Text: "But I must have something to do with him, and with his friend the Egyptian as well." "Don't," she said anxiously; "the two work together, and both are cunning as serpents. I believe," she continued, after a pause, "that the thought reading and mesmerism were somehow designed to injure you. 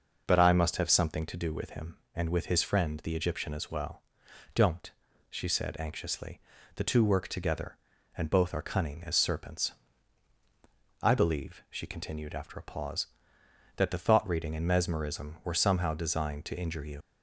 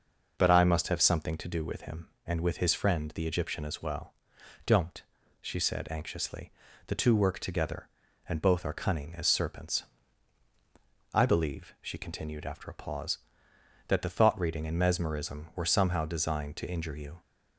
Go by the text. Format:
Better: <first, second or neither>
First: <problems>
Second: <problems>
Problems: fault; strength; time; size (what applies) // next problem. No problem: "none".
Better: second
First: leaves "you" unfinished; at 17.0 s; 85 ms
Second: none